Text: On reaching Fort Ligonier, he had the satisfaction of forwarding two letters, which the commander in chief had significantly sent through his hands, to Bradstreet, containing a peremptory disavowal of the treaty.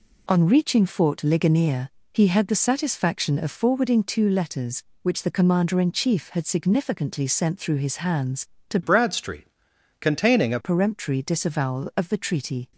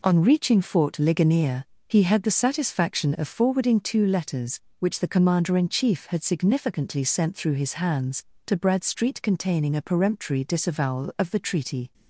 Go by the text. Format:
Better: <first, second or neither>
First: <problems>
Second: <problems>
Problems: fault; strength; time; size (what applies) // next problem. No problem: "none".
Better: second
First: changes voice from "Bradstreet" to "a"; from 8.8 to 10.5 s; 1.7 s long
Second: none